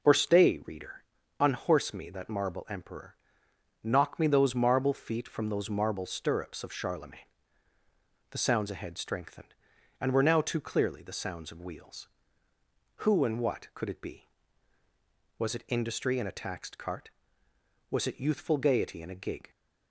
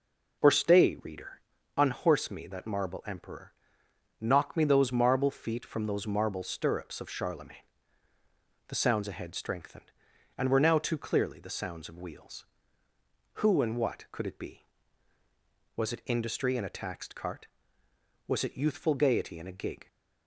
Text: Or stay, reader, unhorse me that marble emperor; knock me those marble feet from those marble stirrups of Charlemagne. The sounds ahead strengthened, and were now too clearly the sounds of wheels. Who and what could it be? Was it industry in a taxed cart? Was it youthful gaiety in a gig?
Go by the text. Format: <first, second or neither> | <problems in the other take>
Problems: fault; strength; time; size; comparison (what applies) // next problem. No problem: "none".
neither | none